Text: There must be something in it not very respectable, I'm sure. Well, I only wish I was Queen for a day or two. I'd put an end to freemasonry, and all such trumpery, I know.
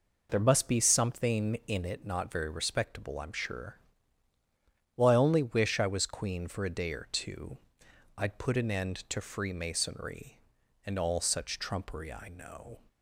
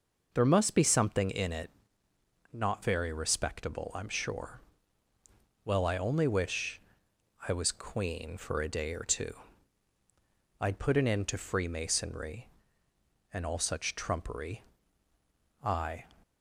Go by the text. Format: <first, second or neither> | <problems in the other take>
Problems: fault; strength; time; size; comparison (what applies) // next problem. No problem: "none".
first | pauses between "it" and "not"; noticeable; at 1.6 s; 0.84 s long // pauses between "wish" and "I"; noticeable; at 6.7 s; 0.68 s long // stops before "know"; at 16.2 s